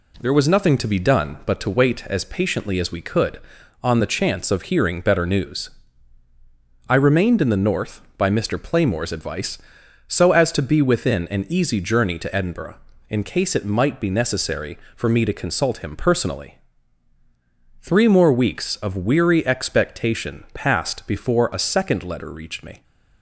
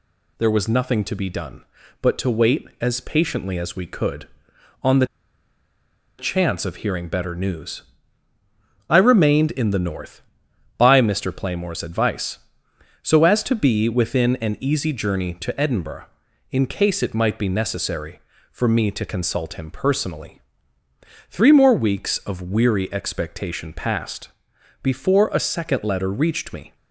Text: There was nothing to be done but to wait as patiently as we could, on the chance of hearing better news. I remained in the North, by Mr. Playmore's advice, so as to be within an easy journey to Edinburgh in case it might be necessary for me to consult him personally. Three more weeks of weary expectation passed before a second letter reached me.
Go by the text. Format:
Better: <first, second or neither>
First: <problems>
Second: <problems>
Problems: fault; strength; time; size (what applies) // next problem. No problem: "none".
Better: first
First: none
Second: pauses between "the" and "chance"; at 5.0 s; 1.1 s long // pauses between "passed" and "before"; noticeable; at 24.2 s; 0.54 s long